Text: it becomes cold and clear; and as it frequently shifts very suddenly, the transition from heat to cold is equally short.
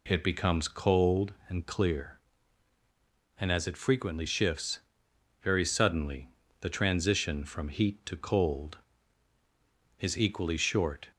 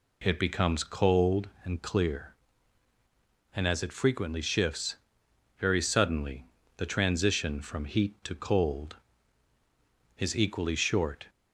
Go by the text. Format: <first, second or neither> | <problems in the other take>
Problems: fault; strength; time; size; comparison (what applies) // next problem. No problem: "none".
neither | pauses between "shifts" and "very"; noticeable; the same in both